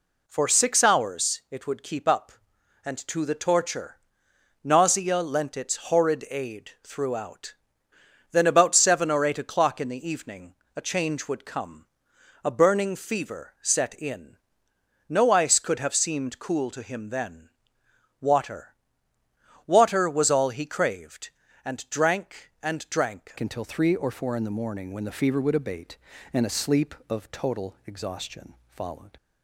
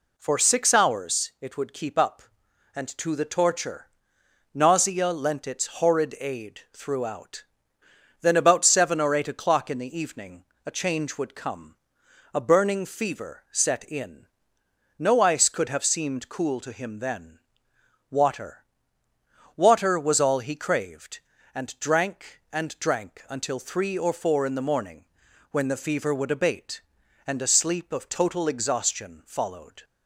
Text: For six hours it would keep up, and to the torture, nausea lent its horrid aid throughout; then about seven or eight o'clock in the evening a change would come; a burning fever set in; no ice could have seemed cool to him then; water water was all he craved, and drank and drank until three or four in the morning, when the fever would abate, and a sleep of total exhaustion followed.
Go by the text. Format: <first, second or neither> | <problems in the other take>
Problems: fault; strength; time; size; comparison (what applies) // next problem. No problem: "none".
second | pauses between "evening" and "a"; slight; at 10.5 s; 0.20 s long; slight in the second // pauses between "water" and "water"; noticeable; at 18.7 s; 0.92 s long; noticeable in the second // changes voice at "until"; from 23.4 s on; 5.7 s long // pauses between "exhaustion" and "followed"; slight; at 28.5 s; 0.20 s long